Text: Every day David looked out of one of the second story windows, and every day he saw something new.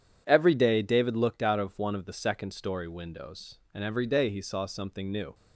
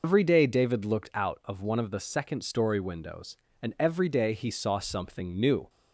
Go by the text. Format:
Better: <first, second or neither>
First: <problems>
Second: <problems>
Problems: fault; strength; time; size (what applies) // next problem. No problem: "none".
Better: first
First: none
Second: loses the start of "Every"; at 0.0 s; 95 ms